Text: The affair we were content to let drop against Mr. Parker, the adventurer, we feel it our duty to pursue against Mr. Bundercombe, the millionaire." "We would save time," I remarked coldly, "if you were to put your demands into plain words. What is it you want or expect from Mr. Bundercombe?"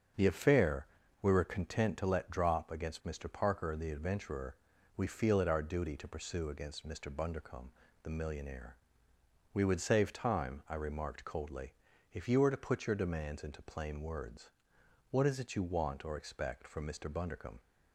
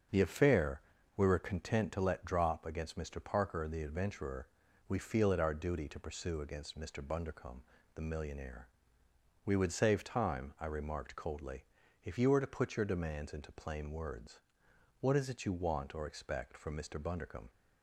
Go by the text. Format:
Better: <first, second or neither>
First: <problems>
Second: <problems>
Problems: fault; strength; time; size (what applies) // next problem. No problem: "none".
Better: neither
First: starts louder than the rest; until 1.5 s; 7 dB // pauses between "affair" and "we"; slight; at 0.8 s; 0.34 s long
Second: starts louder than the rest; until 1.4 s; 7 dB // pauses between "affair" and "we"; slight; at 0.8 s; 0.34 s long